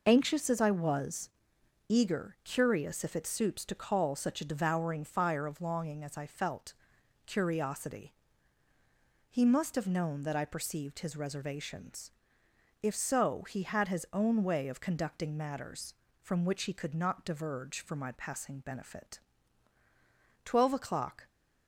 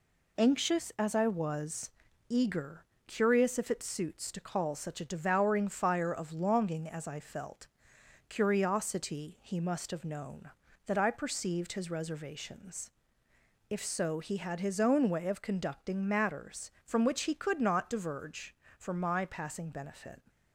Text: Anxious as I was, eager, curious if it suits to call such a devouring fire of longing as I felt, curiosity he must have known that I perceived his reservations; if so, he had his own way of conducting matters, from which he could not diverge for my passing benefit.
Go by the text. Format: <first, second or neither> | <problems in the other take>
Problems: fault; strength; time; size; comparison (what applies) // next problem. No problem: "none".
second | pauses between "curiosity" and "he"; at 8.1 s; 1.1 s long // goes on to say "Twelve o'clock"; noticeable; from 20.4 s on; 0.84 s long